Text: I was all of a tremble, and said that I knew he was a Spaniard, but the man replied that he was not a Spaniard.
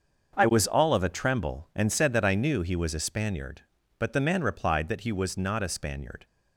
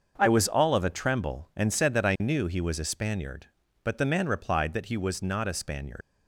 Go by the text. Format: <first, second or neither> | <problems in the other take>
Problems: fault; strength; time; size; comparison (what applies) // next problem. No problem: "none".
first | starts louder than the rest; until 1.1 s; 6.5 dB; also in the first // leaves "Spaniard" unfinished; at 6.0 s; 95 ms